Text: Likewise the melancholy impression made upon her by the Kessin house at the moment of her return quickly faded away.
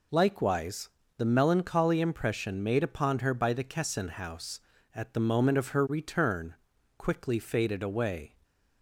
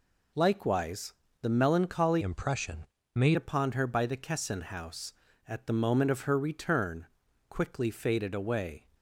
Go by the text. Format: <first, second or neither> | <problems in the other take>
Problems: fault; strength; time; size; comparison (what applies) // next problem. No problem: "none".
first | pauses between "Likewise" and "the"; slight; at 1.1 s; 0.28 s long; slight in the first // changes voice from "impression" to "made"; from 2.2 to 3.3 s; 1.1 s long // pauses between "impression" and "made"; slight; at 2.8 s; 0.30 s long // pauses between "return" and "quickly"; at 7.0 s; 0.44 s long; also in the first